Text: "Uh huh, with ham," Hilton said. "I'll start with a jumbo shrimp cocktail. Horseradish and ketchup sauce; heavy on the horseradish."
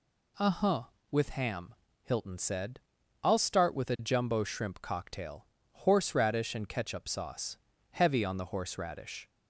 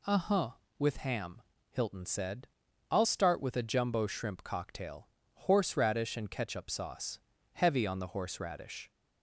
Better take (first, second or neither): neither